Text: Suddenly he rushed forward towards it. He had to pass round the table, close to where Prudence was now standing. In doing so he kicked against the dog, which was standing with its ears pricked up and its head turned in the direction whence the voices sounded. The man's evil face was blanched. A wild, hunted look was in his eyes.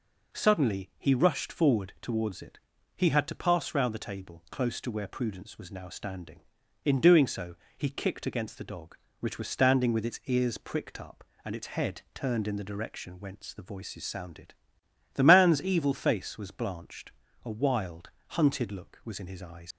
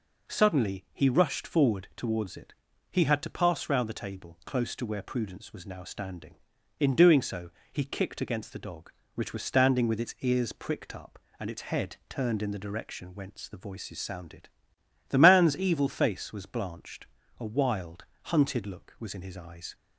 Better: second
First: pauses between "so" and "he"; slight; at 7.5 s; 0.20 s long // leaves "eyes" unfinished; at 19.7 s; 90 ms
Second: pauses between "so" and "he"; slight; at 7.5 s; 0.20 s long

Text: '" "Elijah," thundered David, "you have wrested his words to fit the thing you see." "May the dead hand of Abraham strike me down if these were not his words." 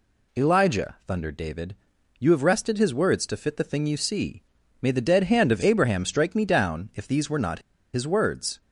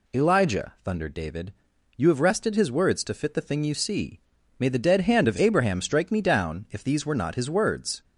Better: second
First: pauses between "not" and "his"; slight; at 7.5 s; 0.35 s long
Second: none

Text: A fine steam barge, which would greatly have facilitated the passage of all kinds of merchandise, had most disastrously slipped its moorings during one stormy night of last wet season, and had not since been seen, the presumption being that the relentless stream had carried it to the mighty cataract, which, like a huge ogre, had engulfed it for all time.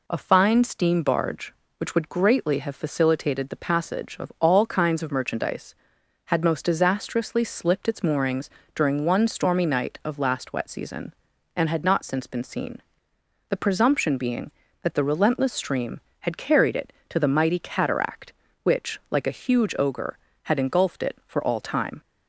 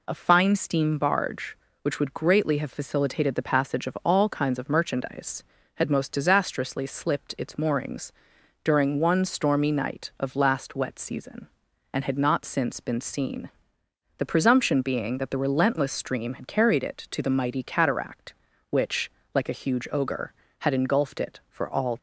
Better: first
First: pauses between "moorings" and "during"; slight; at 8.4 s; 0.28 s long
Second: pauses between "moorings" and "during"; noticeable; at 8.1 s; 0.52 s long // stops before "time"; at 21.9 s

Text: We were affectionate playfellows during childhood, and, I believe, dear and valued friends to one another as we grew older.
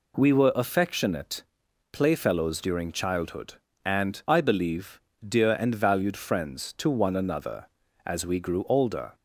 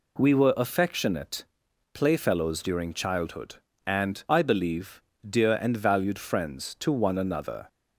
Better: first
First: pauses between "affectionate" and "playfellows"; noticeable; at 1.4 s; 0.48 s long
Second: pauses between "affectionate" and "playfellows"; noticeable; at 1.4 s; 0.48 s long // stops before "as we grew older"; at 7.6 s

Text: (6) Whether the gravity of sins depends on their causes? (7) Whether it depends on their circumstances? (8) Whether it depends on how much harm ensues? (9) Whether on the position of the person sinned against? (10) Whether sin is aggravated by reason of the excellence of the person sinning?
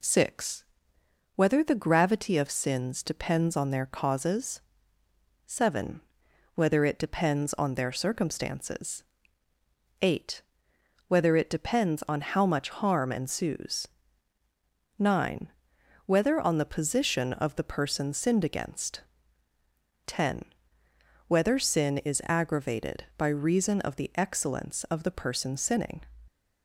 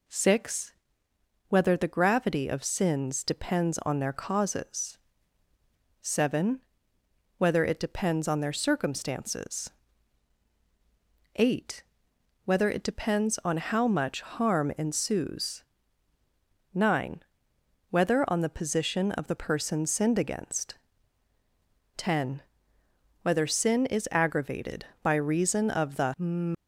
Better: first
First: none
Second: stops before "excellence of the person sinning"; at 26.5 s

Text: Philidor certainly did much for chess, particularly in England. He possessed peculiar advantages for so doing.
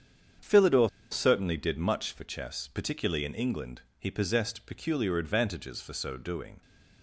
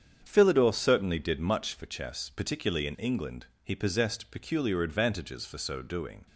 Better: second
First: starts louder than the rest; strong; until 1.6 s; 8 dB // pauses between "Philidor" and "certainly"; slight; at 0.8 s; 0.21 s long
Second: starts louder than the rest; strong; until 1.2 s; 8 dB

